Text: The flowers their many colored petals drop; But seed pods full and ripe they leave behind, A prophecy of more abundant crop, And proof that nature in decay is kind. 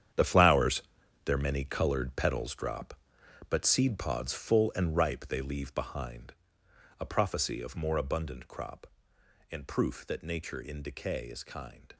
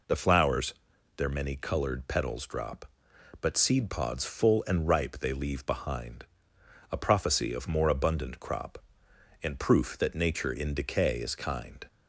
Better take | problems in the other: second | gets quieter; strong; throughout; 12.5 dB // pauses between "flowers" and "their"; at 0.8 s; 0.42 s long; also in the second

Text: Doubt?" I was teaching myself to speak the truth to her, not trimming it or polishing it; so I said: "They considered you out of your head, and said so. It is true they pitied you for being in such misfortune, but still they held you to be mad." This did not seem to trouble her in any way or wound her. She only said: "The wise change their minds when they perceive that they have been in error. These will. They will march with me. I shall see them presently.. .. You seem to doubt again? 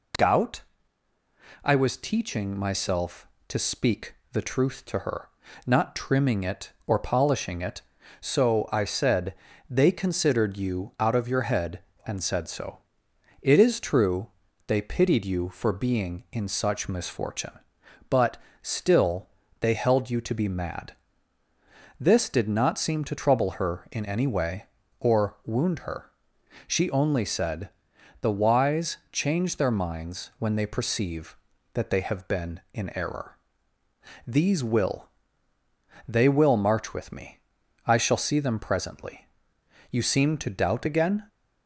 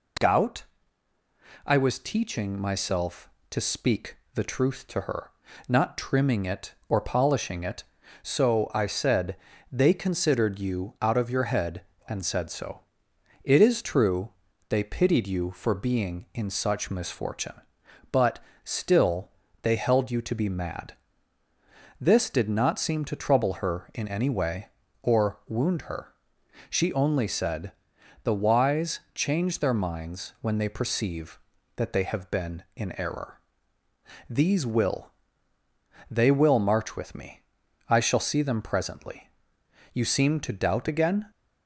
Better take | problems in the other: neither | pauses between "speak" and "the"; slight; the same in both // pauses between "true" and "they"; the same in both // pauses between "but" and "still"; slight; the same in both // pauses between "still" and "they"; slight; the same in both

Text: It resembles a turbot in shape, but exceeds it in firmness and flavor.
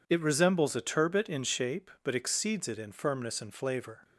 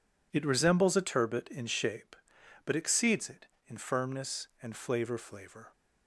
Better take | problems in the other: first | says "flavor" twice; at 5.1 s

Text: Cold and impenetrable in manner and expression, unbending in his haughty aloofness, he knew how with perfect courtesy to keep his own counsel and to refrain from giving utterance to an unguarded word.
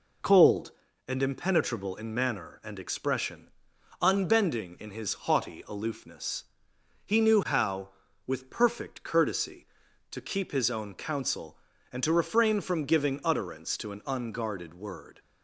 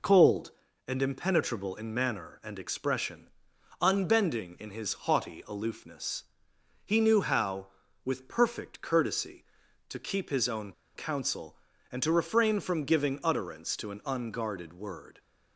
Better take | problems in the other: first | pauses between "own" and "counsel"; slight; at 10.7 s; 0.24 s long

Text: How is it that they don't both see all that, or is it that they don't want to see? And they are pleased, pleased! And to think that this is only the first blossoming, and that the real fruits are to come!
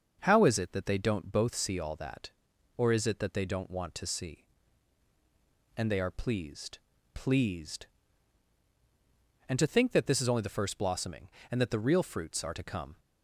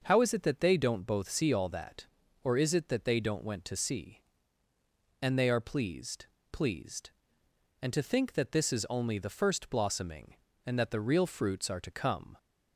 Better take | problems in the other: first | starts louder than the rest; until 1.0 s; 6 dB; also in the first // says "went" for "want"; at 3.4 s

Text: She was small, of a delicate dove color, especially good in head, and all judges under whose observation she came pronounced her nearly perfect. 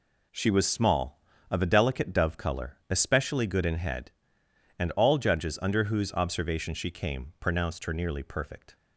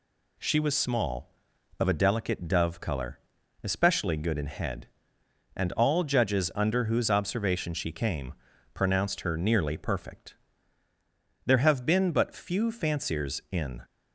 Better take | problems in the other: first | pauses between "came" and "pronounced"; at 8.3 s; 0.40 s long // goes on to say "There have been but few fanciers in"; strong; from 11.4 s on; 2.3 s long

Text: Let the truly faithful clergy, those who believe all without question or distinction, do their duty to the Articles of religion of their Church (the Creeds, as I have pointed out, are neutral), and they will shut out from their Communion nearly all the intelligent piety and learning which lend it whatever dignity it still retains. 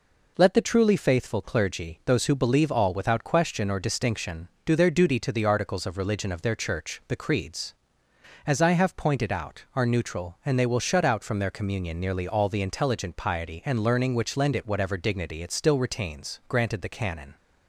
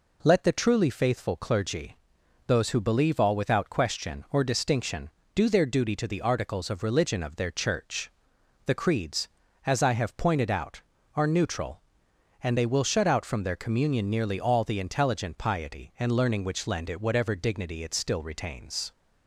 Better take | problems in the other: second | goes on to say "Granted the canon"; noticeable; from 16.4 s on; 0.88 s long

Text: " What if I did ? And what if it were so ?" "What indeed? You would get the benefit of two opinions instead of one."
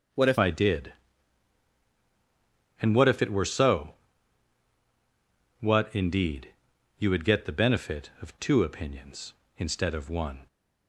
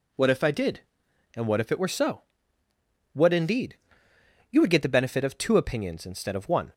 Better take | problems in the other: second | changes voice at "I"; from 0.3 s on; 10.1 s long

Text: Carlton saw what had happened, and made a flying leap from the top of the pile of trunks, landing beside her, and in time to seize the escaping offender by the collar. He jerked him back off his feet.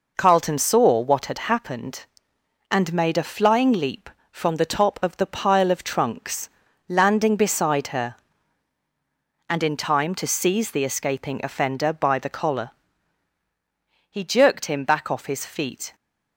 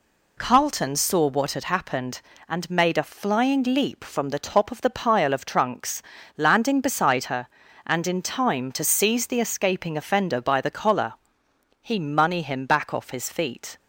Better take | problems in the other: first | says "money" for "jerked"; at 11.9 s

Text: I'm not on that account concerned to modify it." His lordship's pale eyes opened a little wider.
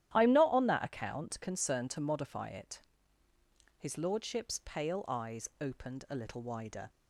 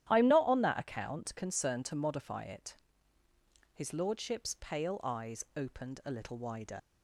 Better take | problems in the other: first | starts louder than the rest; strong; until 1.1 s; 11.5 dB; strong in the first // leaves "wider" unfinished; at 6.7 s; 50 ms

